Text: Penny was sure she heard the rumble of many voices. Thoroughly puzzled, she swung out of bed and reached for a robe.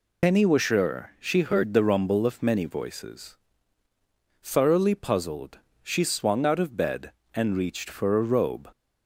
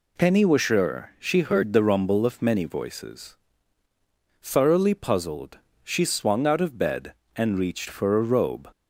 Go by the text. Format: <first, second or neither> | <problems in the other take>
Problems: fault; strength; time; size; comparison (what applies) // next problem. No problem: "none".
second | loses the start of "Penny"; at 0.2 s; 60 ms